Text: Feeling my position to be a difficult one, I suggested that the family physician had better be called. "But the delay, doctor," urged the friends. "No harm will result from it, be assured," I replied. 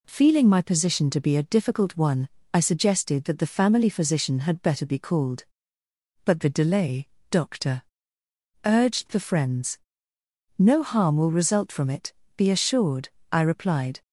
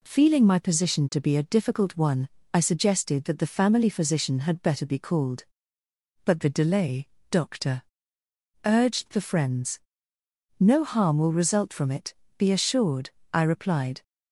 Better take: neither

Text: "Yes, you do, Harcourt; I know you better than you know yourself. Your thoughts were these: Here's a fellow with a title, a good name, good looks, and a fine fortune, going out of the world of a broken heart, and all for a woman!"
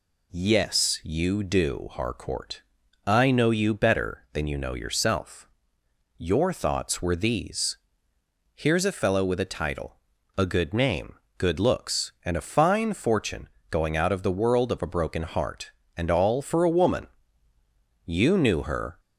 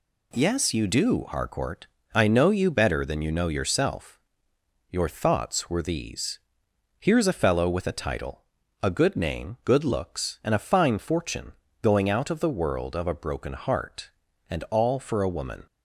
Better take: second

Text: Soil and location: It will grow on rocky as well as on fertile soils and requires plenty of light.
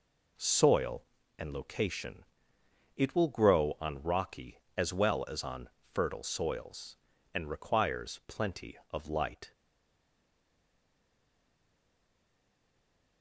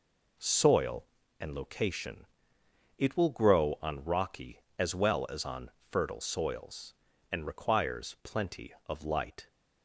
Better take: second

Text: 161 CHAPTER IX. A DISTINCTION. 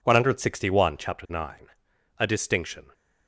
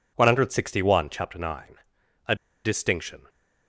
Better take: first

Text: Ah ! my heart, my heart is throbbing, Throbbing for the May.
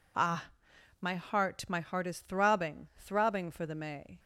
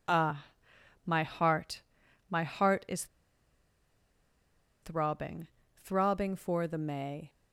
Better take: first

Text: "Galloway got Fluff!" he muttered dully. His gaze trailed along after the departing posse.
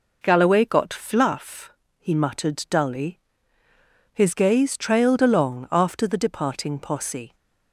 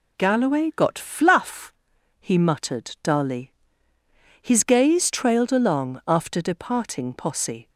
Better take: first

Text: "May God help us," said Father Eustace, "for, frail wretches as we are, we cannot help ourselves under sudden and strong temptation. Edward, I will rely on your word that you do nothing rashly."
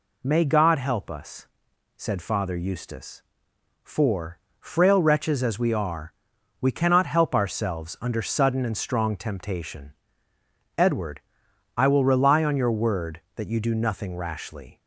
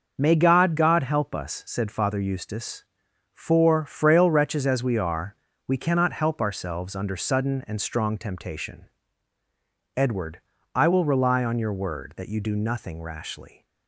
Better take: first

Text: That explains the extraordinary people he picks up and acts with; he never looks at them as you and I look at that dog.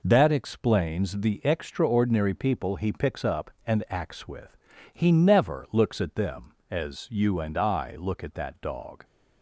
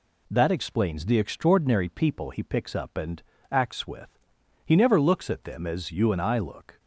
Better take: first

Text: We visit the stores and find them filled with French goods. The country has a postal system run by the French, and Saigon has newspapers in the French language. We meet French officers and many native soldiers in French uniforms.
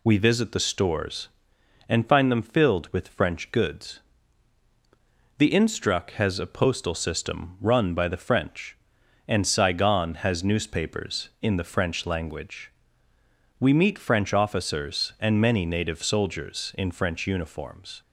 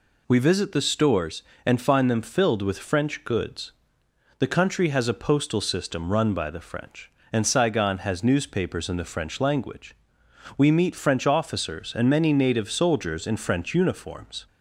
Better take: second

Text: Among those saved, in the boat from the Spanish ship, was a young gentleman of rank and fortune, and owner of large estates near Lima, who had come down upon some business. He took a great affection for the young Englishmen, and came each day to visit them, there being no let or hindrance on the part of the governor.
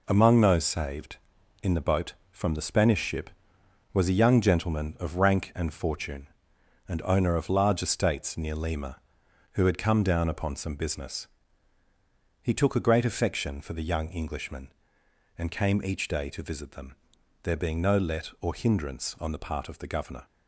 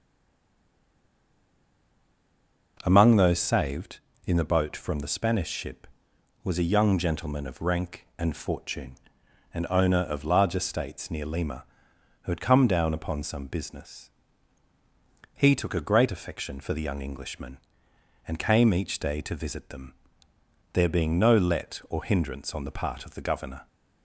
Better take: first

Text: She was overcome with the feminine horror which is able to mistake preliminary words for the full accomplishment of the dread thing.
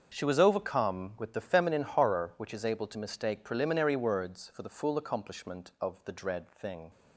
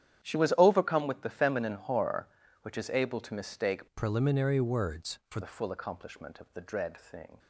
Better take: first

